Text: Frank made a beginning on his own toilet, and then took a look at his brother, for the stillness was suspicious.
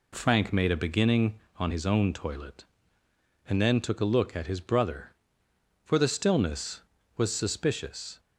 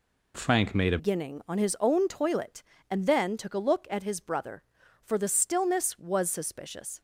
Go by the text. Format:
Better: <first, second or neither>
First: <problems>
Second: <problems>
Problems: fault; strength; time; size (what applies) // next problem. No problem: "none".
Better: first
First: none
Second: changes voice at "beginning"; from 0.9 s on; 6.0 s long